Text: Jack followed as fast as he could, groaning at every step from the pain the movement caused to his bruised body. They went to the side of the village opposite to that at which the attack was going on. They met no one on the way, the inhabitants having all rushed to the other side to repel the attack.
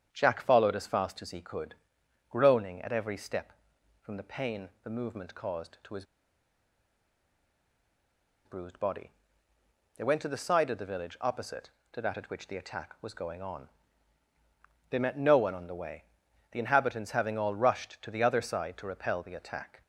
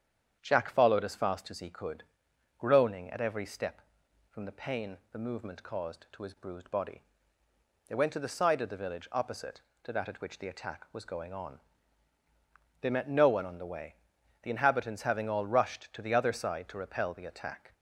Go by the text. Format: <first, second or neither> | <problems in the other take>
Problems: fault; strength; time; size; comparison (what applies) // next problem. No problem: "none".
second | starts louder than the rest; strong; until 1.1 s; 8.5 dB; strong in the second // pauses between "his" and "bruised"; strong; at 6.0 s; 2.4 s long